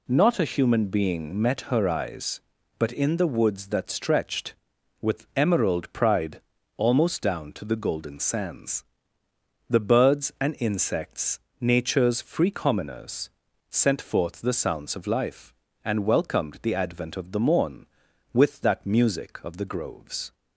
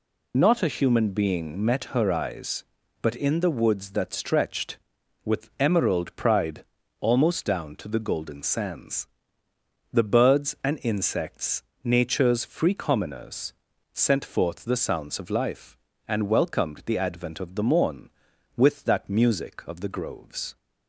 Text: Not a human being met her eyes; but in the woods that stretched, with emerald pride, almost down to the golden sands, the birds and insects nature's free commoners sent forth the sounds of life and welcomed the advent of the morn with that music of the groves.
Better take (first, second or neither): first